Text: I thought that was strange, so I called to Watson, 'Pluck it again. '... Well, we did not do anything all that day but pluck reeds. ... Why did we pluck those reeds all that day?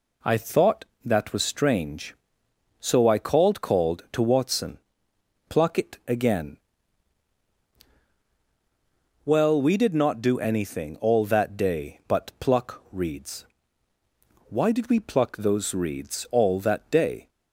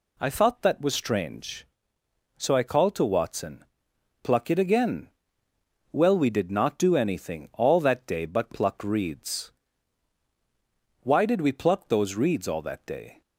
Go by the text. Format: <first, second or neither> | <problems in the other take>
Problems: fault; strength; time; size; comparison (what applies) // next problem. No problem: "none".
second | says "called" twice; at 3.6 s